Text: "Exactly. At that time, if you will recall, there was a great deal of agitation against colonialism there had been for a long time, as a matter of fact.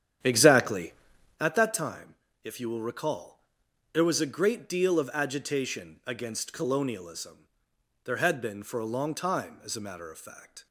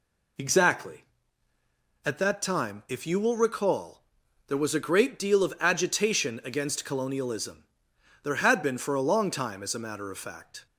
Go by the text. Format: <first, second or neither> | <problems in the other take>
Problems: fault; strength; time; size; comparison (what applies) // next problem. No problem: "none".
second | starts louder than the rest; strong; until 1.5 s; 10 dB // pauses between "colonialism" and "there"; noticeable; at 7.4 s; 0.58 s long; noticeable in the second